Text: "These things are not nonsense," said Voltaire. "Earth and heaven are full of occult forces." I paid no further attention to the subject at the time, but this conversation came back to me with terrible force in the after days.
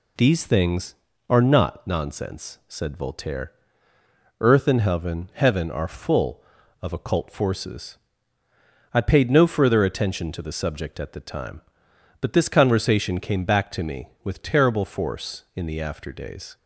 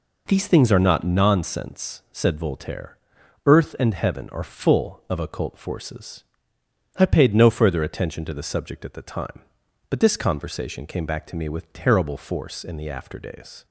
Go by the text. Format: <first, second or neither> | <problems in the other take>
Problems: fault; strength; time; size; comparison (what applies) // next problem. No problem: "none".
second | says "heaven" twice; at 5.3 s